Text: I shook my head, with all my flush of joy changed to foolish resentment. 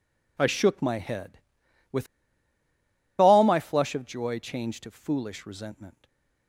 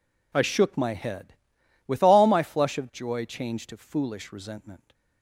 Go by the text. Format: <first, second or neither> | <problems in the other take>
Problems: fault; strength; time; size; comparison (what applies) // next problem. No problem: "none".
second | pauses between "with" and "all"; at 2.0 s; 1.1 s long // stays silent after the last word; slight; from 5.9 s on; 0.5 s long